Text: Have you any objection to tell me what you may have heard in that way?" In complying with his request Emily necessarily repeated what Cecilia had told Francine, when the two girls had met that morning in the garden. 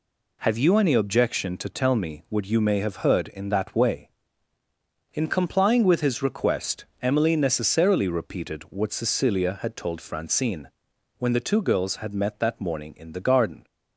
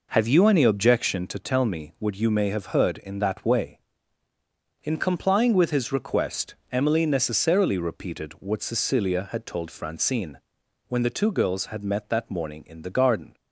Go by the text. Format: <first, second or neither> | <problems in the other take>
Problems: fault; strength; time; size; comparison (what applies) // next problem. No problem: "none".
first | starts louder than the rest; noticeable; until 1.3 s; 5 dB // pauses between "request" and "Emily"; slight; at 6.5 s; 0.16 s long; slight in the first